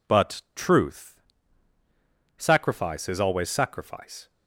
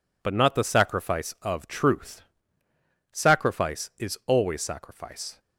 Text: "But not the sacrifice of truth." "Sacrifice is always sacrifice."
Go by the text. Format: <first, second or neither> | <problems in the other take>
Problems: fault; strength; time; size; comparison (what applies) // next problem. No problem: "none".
second | skips "not the sacrifice of"; at 0.4 s